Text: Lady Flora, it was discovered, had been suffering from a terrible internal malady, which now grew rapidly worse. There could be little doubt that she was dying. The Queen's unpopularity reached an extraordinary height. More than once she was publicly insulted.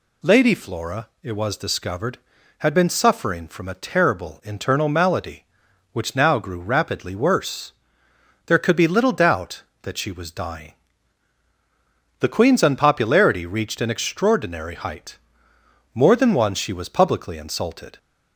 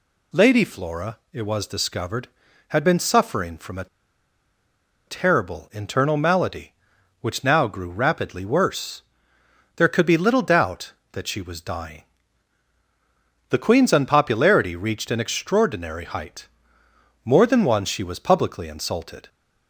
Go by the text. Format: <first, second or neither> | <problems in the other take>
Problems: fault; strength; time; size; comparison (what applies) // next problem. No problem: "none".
first | pauses between "a" and "terrible"; at 3.8 s; 1.2 s long